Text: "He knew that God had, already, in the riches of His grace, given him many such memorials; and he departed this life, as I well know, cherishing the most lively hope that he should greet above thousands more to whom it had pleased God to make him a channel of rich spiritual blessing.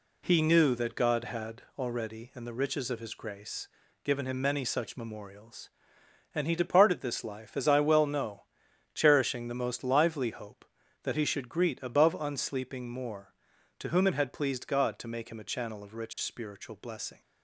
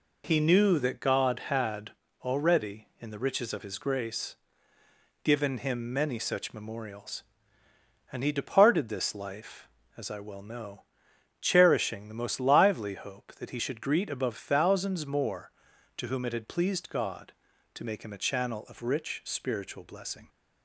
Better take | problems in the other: second | says "unsleeping" for "thousands"; at 12.1 s

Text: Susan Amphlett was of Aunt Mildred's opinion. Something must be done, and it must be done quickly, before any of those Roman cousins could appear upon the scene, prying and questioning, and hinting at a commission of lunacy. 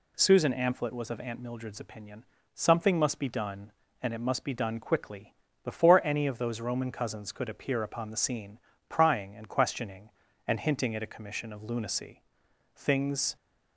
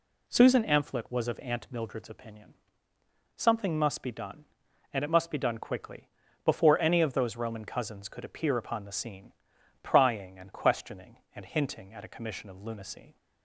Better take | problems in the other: second | goes on to say "Things"; from 12.7 s on; 0.60 s long

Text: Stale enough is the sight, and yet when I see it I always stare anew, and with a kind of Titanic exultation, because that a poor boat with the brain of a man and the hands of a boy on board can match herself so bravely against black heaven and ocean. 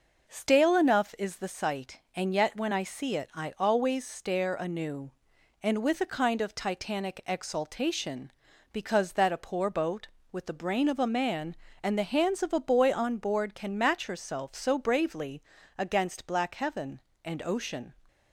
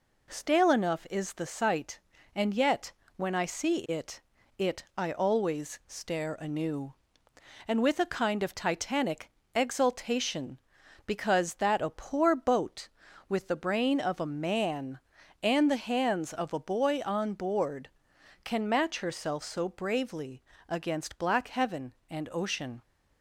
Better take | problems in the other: first | pauses between "yet" and "when"; slight; at 2.9 s; 0.26 s long // says "it" twice; at 4.5 s // pauses between "Titanic" and "exultation"; slight; at 9.2 s; 0.24 s long // pauses between "bravely" and "against"; slight; at 20.4 s; 0.28 s long; slight in the first

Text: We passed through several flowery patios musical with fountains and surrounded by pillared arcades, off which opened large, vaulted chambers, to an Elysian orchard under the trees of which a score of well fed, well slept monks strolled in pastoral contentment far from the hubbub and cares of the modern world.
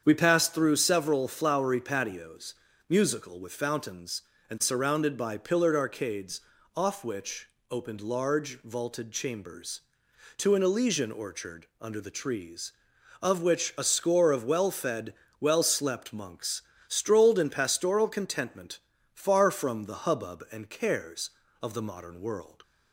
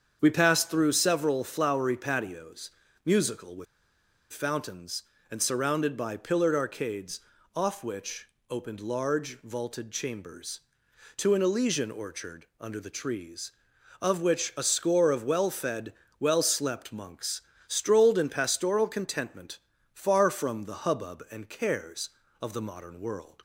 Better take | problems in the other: first | starts louder than the rest; strong; until 1.2 s; 7.5 dB; strong in the first // pauses between "patios" and "musical"; slight; at 2.7 s; 0.36 s long; slight in the first // pauses between "with" and "fountains"; noticeable; at 3.6 s; 0.67 s long // pauses between "which" and "opened"; slight; at 8.2 s; 0.24 s long; slight in the first // pauses between "orchard" and "under"; slight; at 12.4 s; 0.16 s long; slight in the first // pauses between "monks" and "strolled"; slight; at 17.4 s; 0.26 s long; slight in the first // pauses between "contentment" and "far"; at 19.5 s; 0.38 s long; also in the first

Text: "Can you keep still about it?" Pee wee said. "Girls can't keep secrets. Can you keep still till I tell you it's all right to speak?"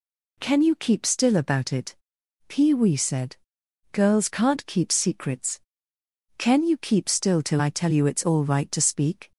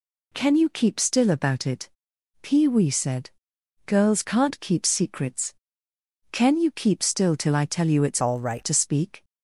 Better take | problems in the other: first | changes voice from "all" to "right"; from 8.2 to 8.6 s; 0.4 s long

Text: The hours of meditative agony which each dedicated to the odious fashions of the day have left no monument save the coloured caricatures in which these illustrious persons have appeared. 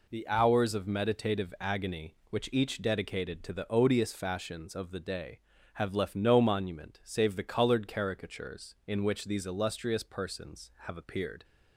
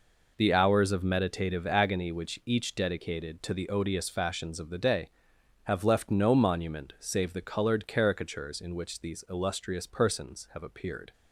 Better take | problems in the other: neither | none

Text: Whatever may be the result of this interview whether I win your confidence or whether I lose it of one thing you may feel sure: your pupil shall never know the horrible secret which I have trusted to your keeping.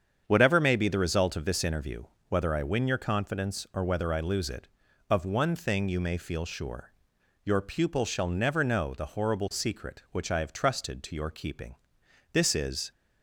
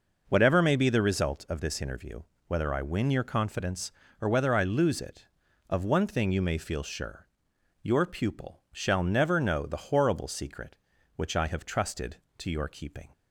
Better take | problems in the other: second | starts louder than the rest; strong; until 1.2 s; 7.5 dB // pauses between "interview" and "whether"; slight; at 2.0 s; 0.26 s long; slight in the second // goes on to say "This is"; from 12.3 s on; 0.58 s long

